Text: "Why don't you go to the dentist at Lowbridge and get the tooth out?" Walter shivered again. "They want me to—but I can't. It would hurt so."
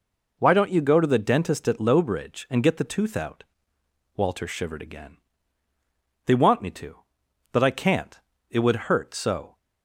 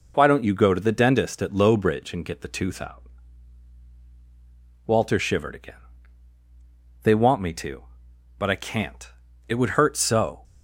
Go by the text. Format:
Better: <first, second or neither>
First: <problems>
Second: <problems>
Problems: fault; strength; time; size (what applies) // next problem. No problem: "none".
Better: neither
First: none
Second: none